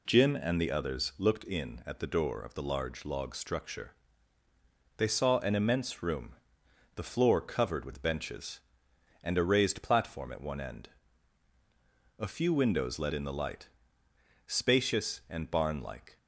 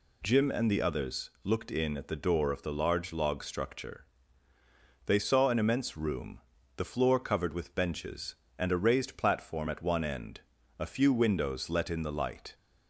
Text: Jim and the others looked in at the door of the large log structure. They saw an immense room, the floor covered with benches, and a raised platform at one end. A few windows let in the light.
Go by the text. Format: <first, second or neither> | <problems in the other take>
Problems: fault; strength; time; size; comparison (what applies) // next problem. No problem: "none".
second | goes on to say "Spacious and barn like"; strong; from 14.4 s on; 1.7 s long